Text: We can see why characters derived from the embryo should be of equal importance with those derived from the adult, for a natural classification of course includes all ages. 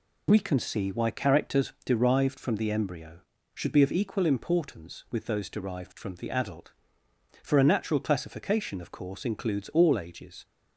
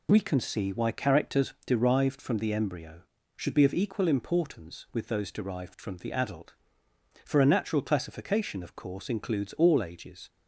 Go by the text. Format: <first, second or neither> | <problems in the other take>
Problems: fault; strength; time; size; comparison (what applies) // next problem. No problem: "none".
neither | none